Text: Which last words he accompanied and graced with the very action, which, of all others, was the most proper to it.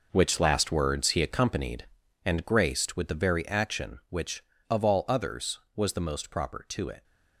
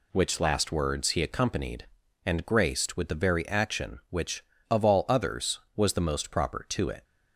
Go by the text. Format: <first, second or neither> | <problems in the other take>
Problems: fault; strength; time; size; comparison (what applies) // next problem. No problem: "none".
second | gets quieter; strong; throughout; 11 dB